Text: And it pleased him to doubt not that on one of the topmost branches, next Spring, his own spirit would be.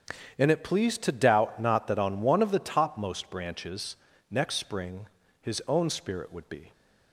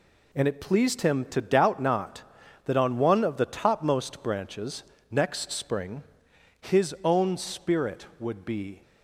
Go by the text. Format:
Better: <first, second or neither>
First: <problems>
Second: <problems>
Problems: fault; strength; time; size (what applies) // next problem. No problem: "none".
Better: second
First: starts louder than the rest; strong; until 1.4 s; 8.5 dB // skips "him"; at 1.0 s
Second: none